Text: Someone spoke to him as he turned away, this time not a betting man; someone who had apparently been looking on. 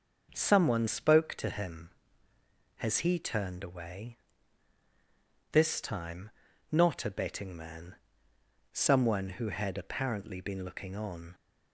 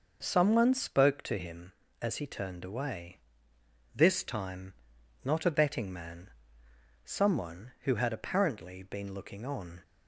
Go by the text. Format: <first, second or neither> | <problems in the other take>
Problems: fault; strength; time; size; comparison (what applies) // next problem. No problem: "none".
second | starts louder than the rest; noticeable; until 1.3 s; 6 dB // says "has" for "as"; at 2.7 s // pauses between "time" and "not"; at 6.3 s; 0.40 s long; noticeable in the second